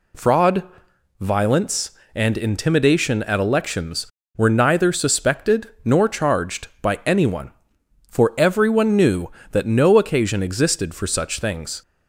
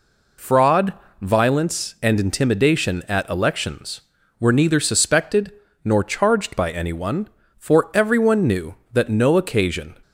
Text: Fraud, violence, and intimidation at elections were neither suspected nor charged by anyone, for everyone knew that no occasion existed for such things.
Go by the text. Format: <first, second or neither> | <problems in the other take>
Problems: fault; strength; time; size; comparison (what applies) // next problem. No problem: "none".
first | pauses between "suspected" and "nor"; slight; at 5.5 s; 0.32 s long // stops before "existed for such things"; at 10.0 s